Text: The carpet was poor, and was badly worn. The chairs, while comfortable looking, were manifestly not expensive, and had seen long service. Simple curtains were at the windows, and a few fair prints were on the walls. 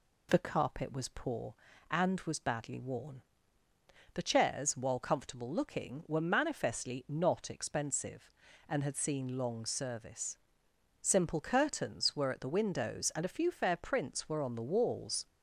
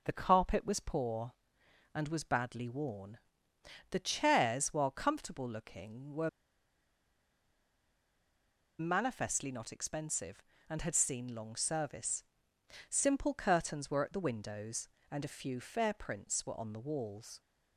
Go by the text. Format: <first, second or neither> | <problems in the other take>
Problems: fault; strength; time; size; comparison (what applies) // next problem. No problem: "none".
first | pauses between "were" and "manifestly"; strong; at 6.2 s; 2.5 s long